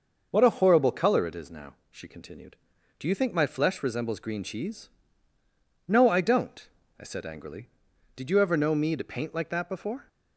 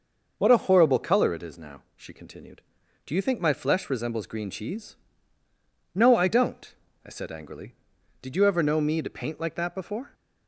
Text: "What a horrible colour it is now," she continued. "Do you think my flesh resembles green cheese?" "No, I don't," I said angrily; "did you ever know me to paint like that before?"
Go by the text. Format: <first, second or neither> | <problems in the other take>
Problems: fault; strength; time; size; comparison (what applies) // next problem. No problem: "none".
neither | none